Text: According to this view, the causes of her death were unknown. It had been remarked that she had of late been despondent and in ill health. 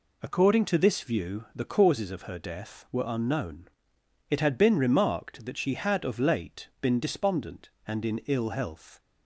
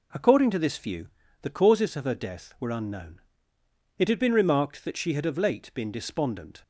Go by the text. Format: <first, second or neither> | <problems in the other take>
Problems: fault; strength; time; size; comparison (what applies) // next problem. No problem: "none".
first | stops before "and in ill health"; at 6.6 s